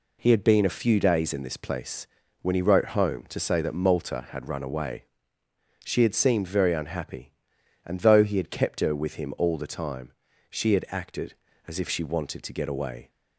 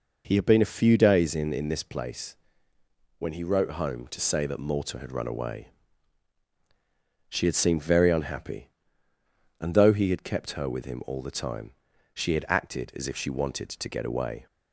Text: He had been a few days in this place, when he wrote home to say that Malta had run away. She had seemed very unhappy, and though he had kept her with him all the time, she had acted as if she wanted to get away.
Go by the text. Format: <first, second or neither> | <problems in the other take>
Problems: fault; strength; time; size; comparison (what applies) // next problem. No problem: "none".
first | says "in" twice; at 1.5 s